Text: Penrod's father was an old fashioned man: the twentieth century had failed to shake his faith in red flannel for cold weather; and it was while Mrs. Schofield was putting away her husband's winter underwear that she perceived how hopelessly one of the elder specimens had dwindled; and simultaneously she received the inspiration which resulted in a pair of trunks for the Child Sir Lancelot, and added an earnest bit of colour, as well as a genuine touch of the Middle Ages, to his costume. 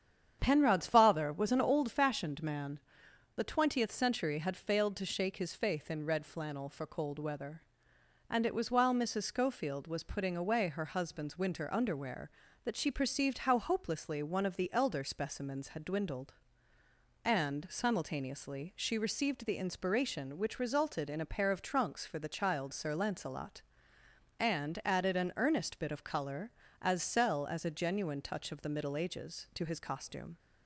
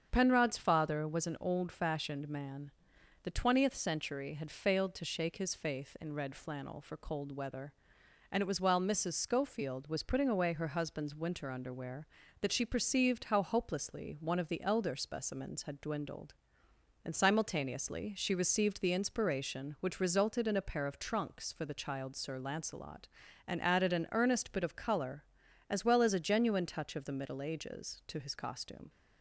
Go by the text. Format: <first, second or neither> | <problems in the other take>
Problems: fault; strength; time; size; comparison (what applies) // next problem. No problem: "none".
second | starts louder than the rest; strong; until 1.4 s; 8.5 dB; strong in the second // says "cell" for "well"; at 27.0 s